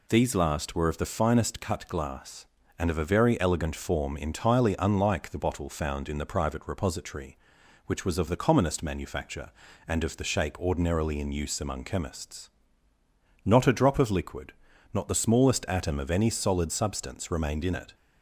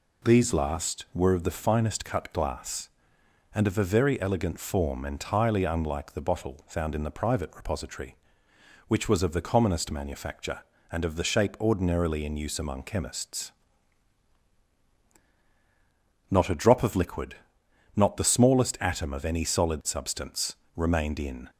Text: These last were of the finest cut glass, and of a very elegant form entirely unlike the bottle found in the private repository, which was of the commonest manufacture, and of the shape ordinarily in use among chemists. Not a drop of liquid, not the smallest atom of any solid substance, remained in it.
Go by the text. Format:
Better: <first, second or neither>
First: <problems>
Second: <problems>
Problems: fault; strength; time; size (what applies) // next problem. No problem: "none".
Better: first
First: none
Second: stops before "it"; at 21.4 s